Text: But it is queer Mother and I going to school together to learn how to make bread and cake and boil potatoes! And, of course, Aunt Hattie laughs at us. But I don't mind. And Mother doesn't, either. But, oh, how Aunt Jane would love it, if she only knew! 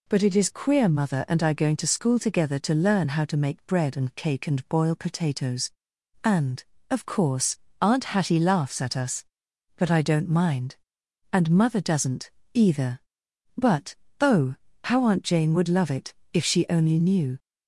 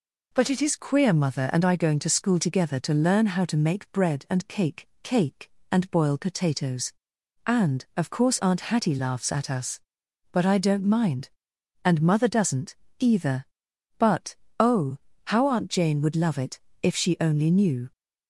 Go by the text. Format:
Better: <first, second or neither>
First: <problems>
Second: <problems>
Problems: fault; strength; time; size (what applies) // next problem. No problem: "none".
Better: first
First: none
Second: says "cake" twice; at 5.0 s